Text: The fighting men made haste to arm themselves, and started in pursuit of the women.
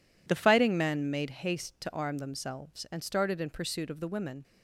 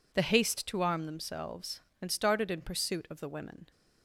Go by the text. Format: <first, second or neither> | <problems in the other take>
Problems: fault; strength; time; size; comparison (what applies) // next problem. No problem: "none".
first | skips "fighting men made"; at 0.2 s